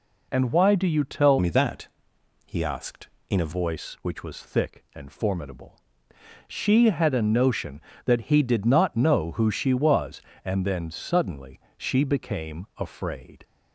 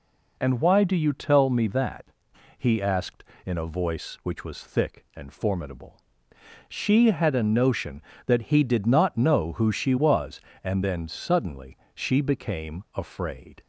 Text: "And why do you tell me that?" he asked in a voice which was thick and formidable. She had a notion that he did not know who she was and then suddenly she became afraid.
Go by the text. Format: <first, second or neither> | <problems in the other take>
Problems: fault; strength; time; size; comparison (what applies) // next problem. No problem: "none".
second | changes voice from "me" to "a"; from 1.3 to 3.5 s; 2.2 s long // pauses between "suddenly" and "she"; slight; at 11.5 s; 0.18 s long; slight in the second